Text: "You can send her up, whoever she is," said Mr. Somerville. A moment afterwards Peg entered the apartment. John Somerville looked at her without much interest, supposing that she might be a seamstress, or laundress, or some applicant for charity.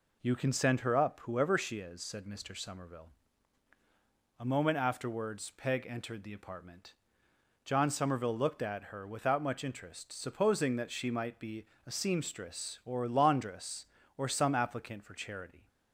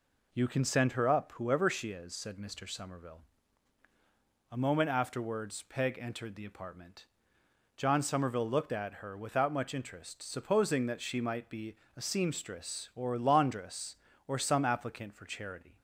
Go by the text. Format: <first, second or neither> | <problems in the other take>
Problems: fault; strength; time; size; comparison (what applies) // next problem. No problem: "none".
neither | pauses between "be" and "a"; slight; the same in both